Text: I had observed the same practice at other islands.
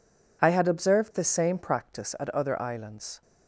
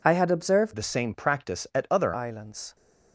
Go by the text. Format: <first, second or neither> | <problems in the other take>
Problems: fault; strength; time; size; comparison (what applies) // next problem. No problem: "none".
first | changes voice from "the" to "other"; from 0.7 to 2.1 s; 1.4 s long